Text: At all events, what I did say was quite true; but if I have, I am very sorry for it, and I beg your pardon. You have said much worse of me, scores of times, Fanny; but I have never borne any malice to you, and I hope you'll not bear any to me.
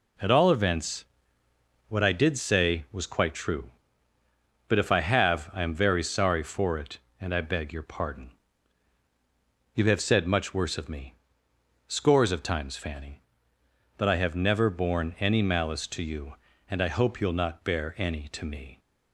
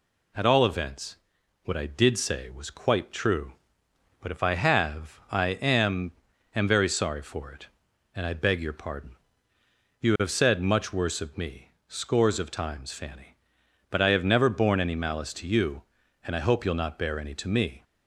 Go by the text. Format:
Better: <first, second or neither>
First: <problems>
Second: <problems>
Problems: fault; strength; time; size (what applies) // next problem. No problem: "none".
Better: first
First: none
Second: says "am" twice; at 6.5 s